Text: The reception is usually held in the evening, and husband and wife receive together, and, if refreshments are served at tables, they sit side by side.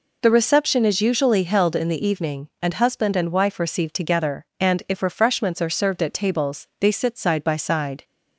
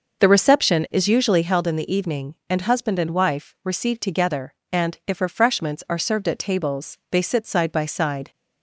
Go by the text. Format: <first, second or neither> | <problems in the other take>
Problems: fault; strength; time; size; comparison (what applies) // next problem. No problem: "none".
first | starts louder than the rest; noticeable; until 1.5 s; 6 dB